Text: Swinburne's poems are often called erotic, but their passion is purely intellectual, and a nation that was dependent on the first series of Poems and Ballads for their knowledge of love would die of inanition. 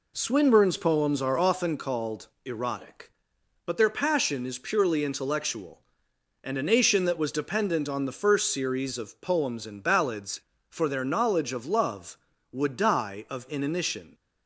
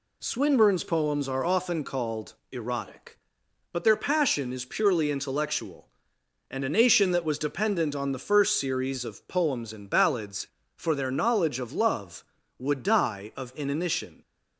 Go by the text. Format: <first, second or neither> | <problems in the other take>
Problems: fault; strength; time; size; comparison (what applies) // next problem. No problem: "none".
second | starts louder than the rest; slight; until 1.8 s; 3 dB // pauses between "called" and "erotic"; slight; at 2.2 s; 0.16 s long; slight in the second